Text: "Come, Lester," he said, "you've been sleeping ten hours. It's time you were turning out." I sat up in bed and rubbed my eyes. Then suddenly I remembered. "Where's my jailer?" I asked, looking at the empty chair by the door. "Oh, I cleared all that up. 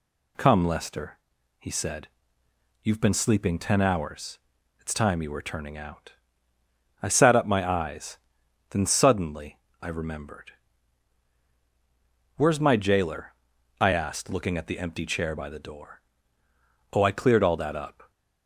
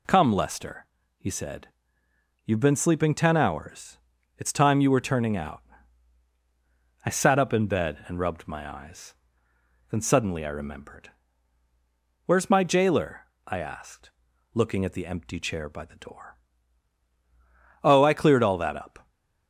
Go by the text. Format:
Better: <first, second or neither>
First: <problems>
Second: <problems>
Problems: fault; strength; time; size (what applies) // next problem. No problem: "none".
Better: second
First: skips "in bed and rubbed"; at 7.4 s // pauses between "suddenly" and "I"; slight; at 9.5 s; 0.22 s long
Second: none